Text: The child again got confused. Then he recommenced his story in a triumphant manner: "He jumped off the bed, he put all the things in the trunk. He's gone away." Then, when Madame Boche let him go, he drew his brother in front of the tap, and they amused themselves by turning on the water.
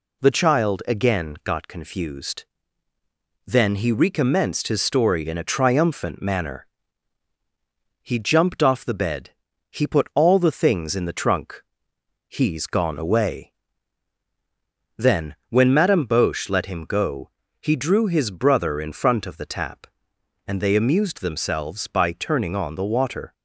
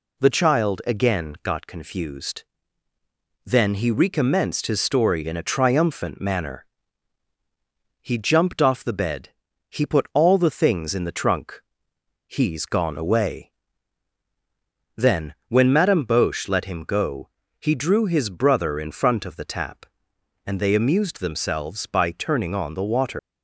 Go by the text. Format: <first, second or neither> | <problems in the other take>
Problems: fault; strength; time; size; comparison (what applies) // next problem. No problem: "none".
first | leaves "water" unfinished; at 23.1 s; 125 ms